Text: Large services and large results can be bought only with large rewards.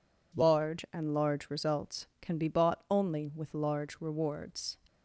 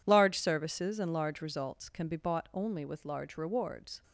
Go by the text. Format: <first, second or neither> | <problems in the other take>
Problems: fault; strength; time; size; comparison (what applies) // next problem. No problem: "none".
second | skips "services"; at 0.8 s